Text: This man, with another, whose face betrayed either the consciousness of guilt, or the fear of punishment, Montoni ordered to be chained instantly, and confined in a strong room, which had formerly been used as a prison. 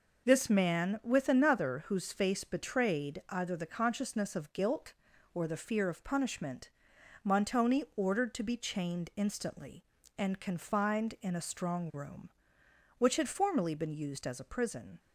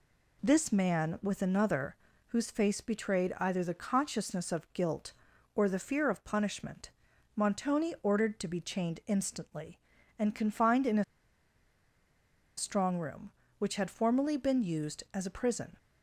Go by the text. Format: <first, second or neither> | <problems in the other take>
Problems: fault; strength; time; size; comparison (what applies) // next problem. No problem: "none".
first | pauses between "a" and "strong"; strong; at 11.0 s; 1.5 s long